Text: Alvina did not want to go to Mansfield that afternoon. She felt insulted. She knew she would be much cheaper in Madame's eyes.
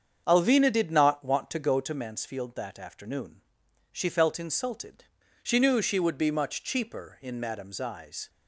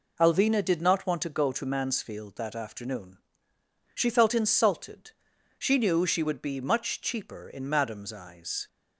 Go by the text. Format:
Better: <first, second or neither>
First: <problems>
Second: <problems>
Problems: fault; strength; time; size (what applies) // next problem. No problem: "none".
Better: second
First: starts louder than the rest; strong; until 2.0 s; 7.5 dB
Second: none